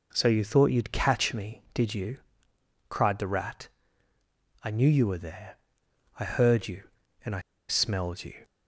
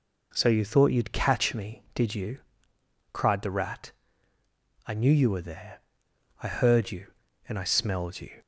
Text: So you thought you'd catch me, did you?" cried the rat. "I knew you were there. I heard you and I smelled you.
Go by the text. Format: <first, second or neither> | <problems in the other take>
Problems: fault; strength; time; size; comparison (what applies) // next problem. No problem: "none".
second | pauses between "I" and "smelled"; slight; at 7.3 s; 0.29 s long